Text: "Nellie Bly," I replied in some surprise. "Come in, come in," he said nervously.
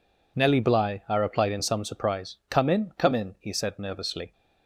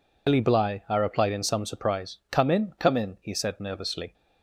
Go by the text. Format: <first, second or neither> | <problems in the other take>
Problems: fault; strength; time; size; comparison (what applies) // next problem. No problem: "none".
first | loses the start of "Nellie"; at 0.2 s; 105 ms